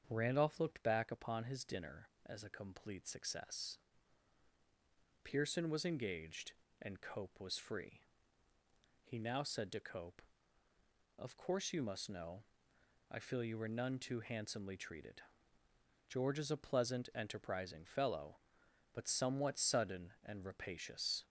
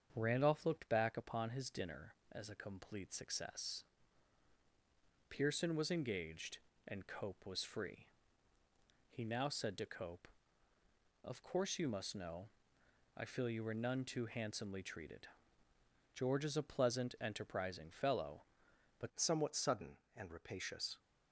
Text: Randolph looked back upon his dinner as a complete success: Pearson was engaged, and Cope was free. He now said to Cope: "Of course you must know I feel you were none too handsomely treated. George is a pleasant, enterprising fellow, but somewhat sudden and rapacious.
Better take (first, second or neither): first